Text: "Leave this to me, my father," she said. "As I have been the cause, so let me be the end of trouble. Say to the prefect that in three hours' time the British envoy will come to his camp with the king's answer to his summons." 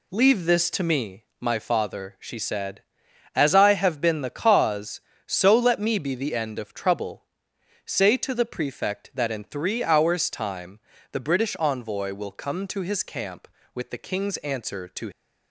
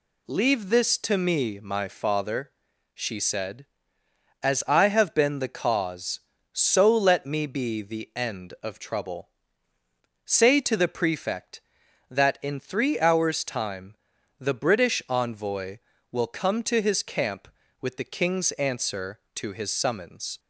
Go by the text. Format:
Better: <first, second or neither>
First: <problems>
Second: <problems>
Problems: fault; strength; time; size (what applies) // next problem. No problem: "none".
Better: second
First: pauses between "time" and "the"; slight; at 10.7 s; 0.32 s long // stops before "his summons"; at 15.1 s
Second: pauses between "time" and "the"; at 13.9 s; 0.42 s long